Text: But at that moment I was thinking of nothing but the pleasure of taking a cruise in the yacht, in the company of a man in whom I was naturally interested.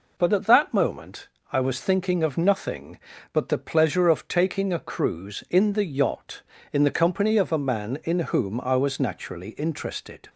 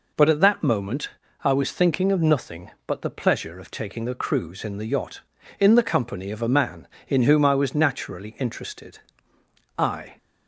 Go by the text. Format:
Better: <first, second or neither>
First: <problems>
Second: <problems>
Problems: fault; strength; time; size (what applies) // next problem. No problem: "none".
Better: first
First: pauses between "moment" and "I"; slight; at 1.2 s; 0.24 s long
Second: pauses between "moment" and "I"; slight; at 1.0 s; 0.34 s long // goes on to say "I"; slight; from 9.7 s on; 0.40 s long